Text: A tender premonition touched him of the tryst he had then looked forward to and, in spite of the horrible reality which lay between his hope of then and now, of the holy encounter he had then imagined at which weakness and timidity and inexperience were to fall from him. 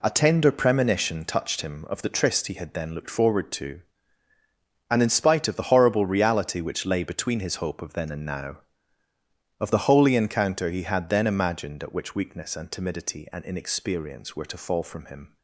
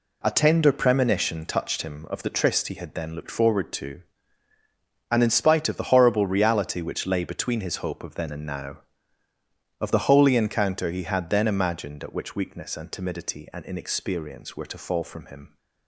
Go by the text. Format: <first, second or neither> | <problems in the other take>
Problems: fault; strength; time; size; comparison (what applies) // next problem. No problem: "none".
neither | none